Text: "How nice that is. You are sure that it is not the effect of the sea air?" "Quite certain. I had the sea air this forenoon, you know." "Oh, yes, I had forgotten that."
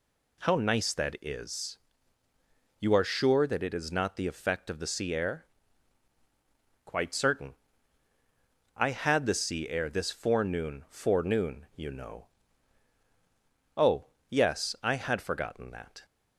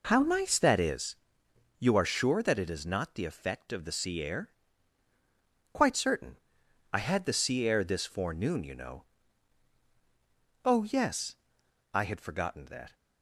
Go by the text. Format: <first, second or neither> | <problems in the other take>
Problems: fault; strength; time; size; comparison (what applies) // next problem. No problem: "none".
second | says "forenoon" twice; at 10.8 s